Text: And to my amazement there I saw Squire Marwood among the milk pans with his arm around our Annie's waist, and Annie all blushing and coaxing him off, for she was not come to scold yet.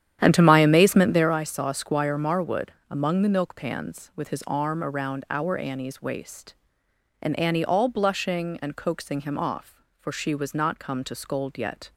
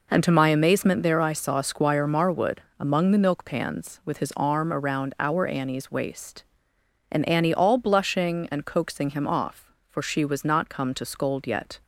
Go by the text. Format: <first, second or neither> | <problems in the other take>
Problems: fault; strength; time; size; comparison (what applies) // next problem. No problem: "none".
second | starts louder than the rest; strong; until 1.4 s; 10.5 dB // pauses between "Marwood" and "among"; slight; at 2.6 s; 0.20 s long; slight in the second